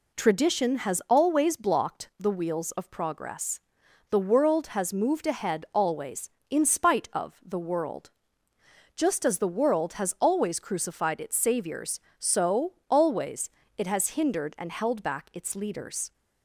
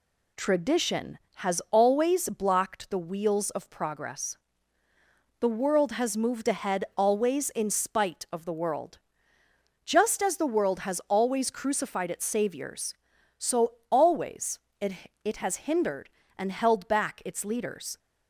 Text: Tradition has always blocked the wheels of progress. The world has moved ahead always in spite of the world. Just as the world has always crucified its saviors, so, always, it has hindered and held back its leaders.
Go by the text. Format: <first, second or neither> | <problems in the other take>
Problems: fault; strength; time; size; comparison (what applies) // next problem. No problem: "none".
first | says "it" twice; at 15.2 s